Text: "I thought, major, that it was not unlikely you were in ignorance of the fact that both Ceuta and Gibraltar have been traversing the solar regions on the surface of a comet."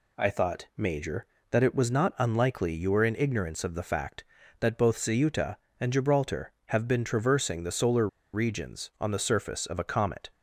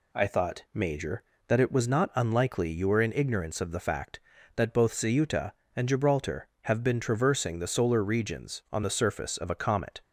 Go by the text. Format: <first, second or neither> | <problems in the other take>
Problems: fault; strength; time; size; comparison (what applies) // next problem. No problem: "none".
second | pauses between "solar" and "regions"; slight; at 8.0 s; 0.26 s long